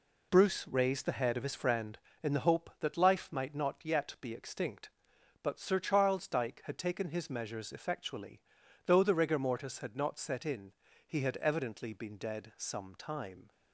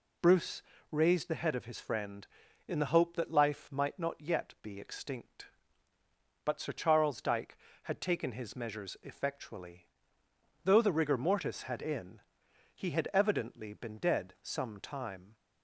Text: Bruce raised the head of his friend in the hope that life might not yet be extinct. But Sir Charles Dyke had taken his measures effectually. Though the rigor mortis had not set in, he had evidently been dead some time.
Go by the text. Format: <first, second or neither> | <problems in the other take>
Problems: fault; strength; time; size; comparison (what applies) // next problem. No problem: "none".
first | pauses between "Bruce" and "raised"; slight; at 0.6 s; 0.28 s long // skips "not set"; at 11.8 s